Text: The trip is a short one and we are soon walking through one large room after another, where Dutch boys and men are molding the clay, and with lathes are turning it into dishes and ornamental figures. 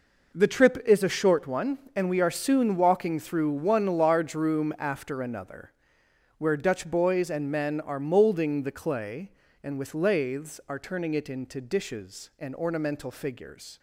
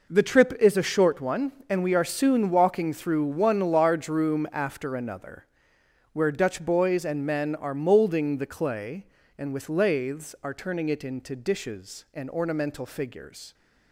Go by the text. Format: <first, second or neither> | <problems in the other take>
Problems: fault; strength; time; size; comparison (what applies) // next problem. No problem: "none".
neither | none